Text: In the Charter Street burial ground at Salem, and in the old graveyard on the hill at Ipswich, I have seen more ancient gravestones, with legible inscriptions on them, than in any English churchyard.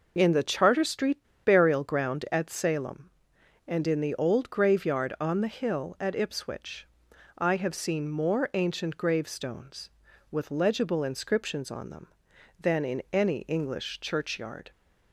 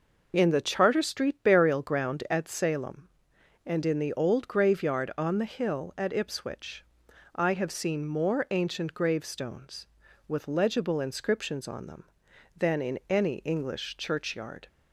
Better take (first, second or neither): second